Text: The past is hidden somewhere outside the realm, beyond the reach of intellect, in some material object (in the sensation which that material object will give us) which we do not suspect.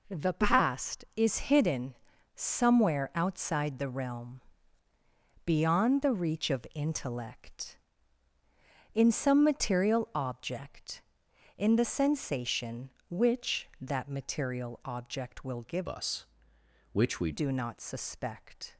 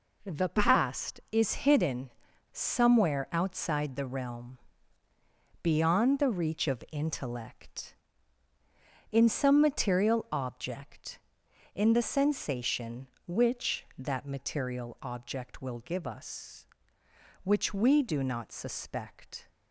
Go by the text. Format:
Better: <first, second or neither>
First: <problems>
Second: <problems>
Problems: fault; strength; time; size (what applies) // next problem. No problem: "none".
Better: second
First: pauses between "hidden" and "somewhere"; at 1.9 s; 0.40 s long // changes voice from "us" to "we"; from 15.8 to 17.3 s; 1.5 s long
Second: pauses between "hidden" and "somewhere"; at 2.1 s; 0.41 s long